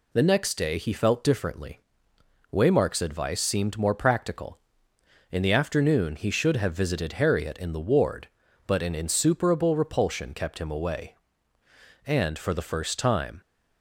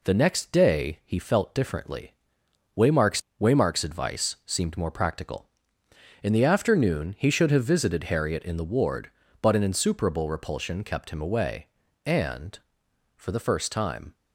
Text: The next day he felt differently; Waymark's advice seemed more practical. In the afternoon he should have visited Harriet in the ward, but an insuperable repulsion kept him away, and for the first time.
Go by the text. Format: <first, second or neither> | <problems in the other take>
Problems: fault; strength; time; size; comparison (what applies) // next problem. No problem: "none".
first | says "Waymark's" twice; at 3.3 s